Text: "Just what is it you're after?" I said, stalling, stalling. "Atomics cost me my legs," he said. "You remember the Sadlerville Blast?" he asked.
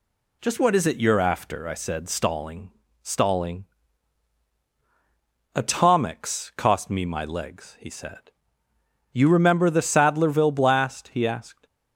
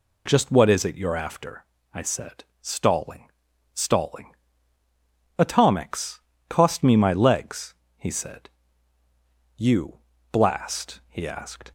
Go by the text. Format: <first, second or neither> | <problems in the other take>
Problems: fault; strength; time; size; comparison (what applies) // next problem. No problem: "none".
first | pauses between "Atomics" and "cost"; slight; at 6.1 s; 0.30 s long // skips "remember the Sadlerville"; at 10.1 s